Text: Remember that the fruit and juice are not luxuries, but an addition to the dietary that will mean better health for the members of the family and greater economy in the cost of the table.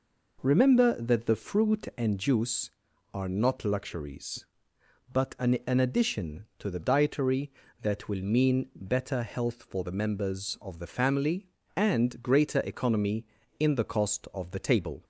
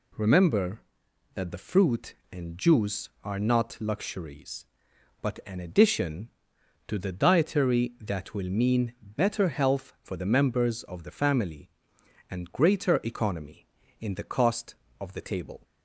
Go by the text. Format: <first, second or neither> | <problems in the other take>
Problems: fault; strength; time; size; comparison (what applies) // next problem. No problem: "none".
second | says "an" twice; at 5.6 s